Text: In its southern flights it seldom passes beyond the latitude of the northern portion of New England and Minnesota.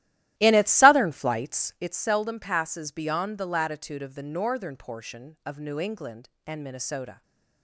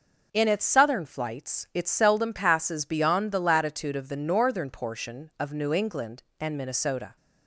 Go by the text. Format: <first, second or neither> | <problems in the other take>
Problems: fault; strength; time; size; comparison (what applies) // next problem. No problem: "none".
second | starts louder than the rest; strong; until 1.9 s; 14.5 dB // stays silent after the last word; slight; from 7.1 s on; 0.5 s long